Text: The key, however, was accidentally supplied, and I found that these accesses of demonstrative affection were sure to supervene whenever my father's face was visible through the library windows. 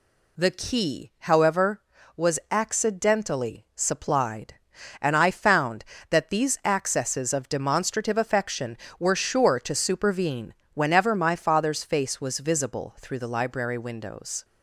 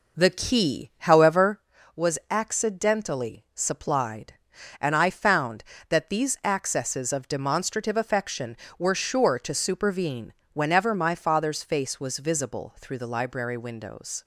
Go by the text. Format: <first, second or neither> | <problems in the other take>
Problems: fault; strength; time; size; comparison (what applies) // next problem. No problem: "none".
first | starts louder than the rest; noticeable; until 1.7 s; 5 dB // pauses between "supervene" and "whenever"; slight; at 10.3 s; 0.22 s long; slight in the first